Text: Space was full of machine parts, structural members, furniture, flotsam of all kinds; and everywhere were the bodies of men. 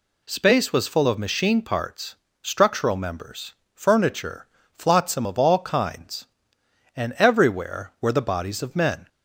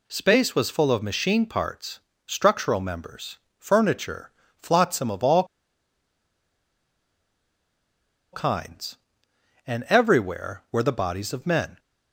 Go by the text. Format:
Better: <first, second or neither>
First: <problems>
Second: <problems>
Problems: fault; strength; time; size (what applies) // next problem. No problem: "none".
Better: first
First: none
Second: pauses between "all" and "kinds"; strong; at 5.4 s; 2.8 s long